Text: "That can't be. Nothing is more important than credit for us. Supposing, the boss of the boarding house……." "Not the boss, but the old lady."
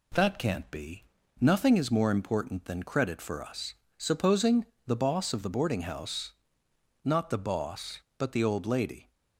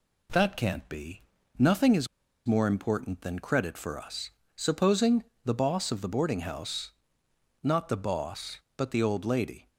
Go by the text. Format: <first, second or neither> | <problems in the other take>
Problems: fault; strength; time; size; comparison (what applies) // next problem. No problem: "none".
first | pauses between "is" and "more"; at 2.0 s; 0.39 s long